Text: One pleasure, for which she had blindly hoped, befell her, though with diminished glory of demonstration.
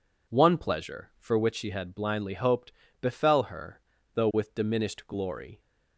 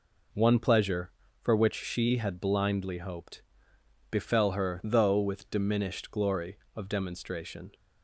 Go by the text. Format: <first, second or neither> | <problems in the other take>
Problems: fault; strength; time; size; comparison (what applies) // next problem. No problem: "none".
second | stops before "of demonstration"; at 5.5 s